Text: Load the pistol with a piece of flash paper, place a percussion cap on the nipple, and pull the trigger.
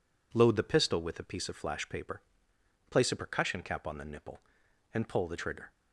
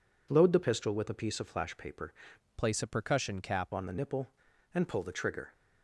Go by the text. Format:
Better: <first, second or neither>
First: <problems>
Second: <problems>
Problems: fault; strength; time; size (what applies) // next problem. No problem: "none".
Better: first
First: none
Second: changes voice from "place" to "cap"; from 2.5 to 3.7 s; 1.2 s long